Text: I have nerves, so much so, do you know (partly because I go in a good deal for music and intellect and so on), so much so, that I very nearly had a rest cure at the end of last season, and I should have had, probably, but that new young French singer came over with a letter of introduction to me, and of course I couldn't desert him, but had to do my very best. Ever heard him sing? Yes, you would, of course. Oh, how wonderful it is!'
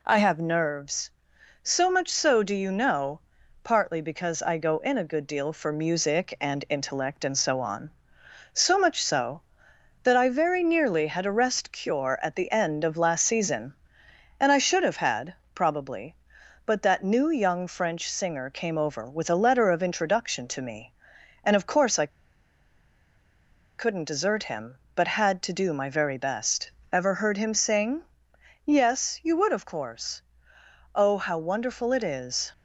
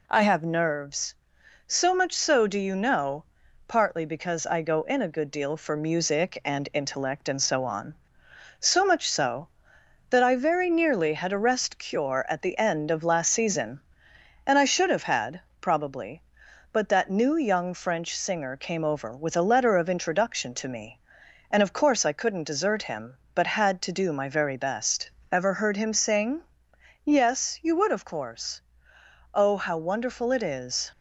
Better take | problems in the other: second | pauses between "I" and "couldn't"; strong; at 22.1 s; 1.6 s long

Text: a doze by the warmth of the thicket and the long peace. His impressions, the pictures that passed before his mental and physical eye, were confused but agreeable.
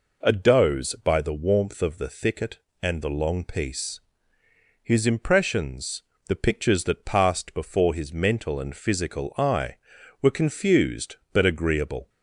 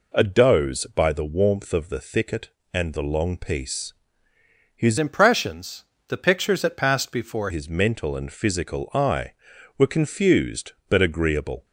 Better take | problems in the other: first | changes voice from "impressions" to "before"; from 4.9 to 7.4 s; 2.5 s long

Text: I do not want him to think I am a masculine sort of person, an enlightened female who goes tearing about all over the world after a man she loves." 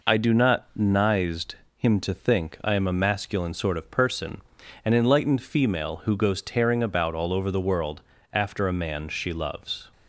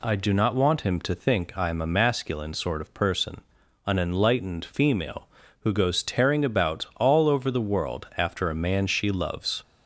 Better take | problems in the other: second | says "nized" for "want"; at 0.7 s // pauses between "world" and "after"; slight; at 8.0 s; 0.32 s long

